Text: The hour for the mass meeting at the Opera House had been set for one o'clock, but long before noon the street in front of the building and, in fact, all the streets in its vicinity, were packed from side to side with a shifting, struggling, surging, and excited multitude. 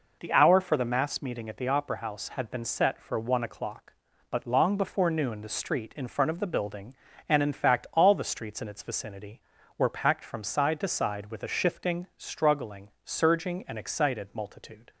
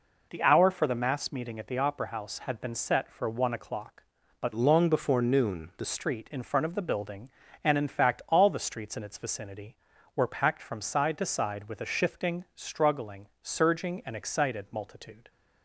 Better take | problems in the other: first | changes voice from "long" to "the"; from 4.5 to 5.8 s; 1.3 s long

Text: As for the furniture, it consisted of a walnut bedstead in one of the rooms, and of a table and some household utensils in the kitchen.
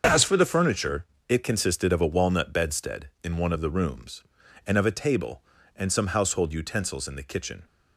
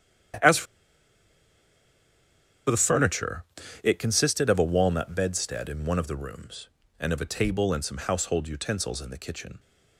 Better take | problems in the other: first | starts louder than the rest; strong; until 3.8 s; 9.5 dB; also in the first // pauses between "for" and "the"; strong; at 0.6 s; 2.0 s long

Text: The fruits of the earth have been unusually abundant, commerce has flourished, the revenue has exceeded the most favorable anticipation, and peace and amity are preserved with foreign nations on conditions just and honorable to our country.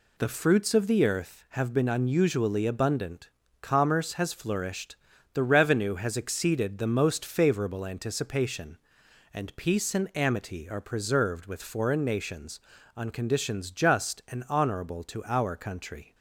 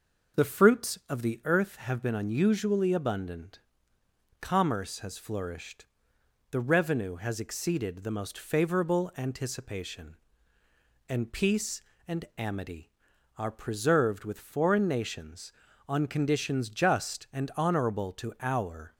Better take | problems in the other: first | stops before "country"; at 18.9 s

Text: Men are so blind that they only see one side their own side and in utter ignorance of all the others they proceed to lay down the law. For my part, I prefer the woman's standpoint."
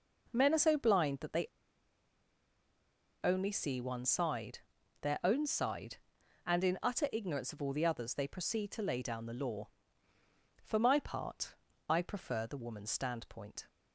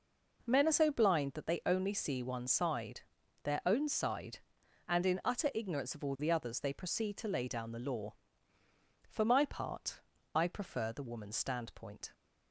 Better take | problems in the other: second | pauses between "they" and "only"; strong; at 1.4 s; 1.7 s long // pauses between "side" and "their"; at 4.5 s; 0.42 s long; also in the second

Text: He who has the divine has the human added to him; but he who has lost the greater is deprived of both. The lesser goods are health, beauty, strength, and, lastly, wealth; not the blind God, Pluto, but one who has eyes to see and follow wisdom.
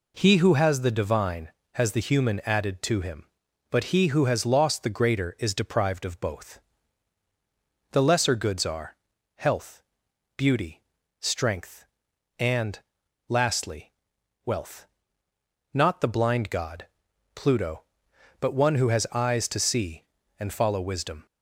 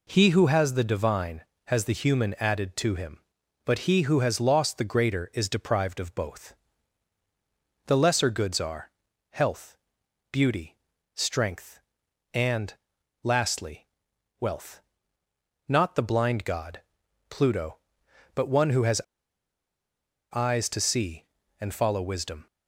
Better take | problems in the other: first | pauses between "are" and "health"; at 8.9 s; 0.42 s long; also in the first // pauses between "has" and "eyes"; strong; at 19.0 s; 1.3 s long

